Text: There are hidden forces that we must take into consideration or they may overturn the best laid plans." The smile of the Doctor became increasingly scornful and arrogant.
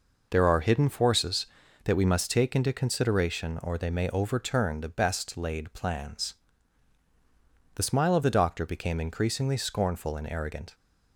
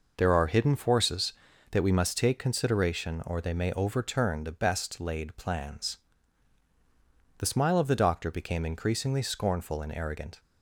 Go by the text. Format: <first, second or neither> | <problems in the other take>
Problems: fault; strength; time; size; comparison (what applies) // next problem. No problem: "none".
first | skips "into"; at 2.3 s